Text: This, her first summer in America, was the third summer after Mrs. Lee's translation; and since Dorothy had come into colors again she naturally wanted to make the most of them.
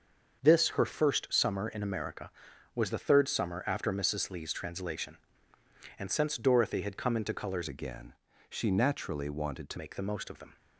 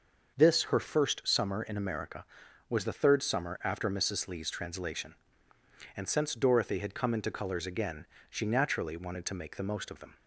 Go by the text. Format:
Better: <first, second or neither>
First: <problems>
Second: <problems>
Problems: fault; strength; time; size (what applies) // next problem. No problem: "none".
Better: second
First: starts louder than the rest; until 1.4 s; 6.5 dB // changes voice from "again" to "to"; from 7.6 to 9.7 s; 2.1 s long // pauses between "again" and "she"; slight; at 8.1 s; 0.34 s long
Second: starts louder than the rest; noticeable; until 1.3 s; 6 dB // pauses between "again" and "she"; slight; at 8.0 s; 0.24 s long